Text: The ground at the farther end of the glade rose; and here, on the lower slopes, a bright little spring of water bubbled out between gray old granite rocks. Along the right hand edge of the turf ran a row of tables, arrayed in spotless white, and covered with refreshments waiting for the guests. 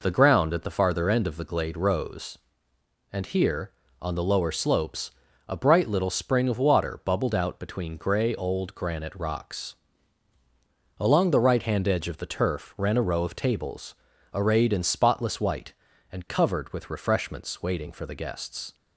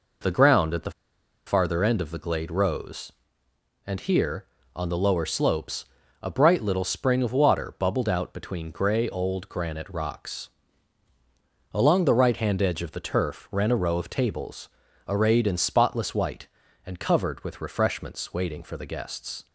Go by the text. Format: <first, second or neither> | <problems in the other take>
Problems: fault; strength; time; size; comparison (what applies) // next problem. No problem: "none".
first | pauses between "the" and "farther"; noticeable; at 0.9 s; 0.56 s long